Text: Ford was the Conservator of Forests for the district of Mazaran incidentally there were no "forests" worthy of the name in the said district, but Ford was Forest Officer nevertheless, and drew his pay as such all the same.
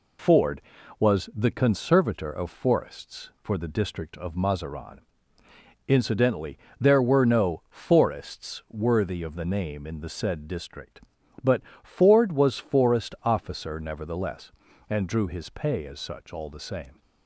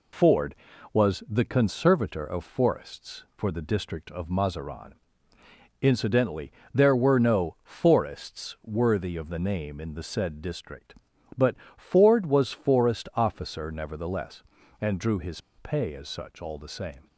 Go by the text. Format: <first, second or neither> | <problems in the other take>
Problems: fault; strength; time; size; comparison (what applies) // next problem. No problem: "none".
first | pauses between "Mazaran" and "incidentally"; noticeable; at 4.9 s; 0.90 s long; noticeable in the first // pauses between "incidentally" and "there"; slight; at 6.5 s; 0.20 s long; slight in the first // pauses between "but" and "Ford"; slight; at 11.5 s; 0.20 s long; slight in the first // pauses between "his" and "pay"; slight; at 15.3 s; 0.18 s long